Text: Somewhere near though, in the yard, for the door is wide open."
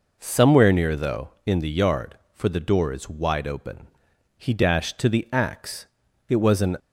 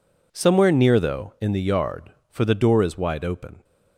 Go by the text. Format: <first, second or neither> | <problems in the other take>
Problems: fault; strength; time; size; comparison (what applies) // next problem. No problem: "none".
second | goes on to say "He dashed to the axe it was an"; strong; from 4.3 s on; 2.4 s long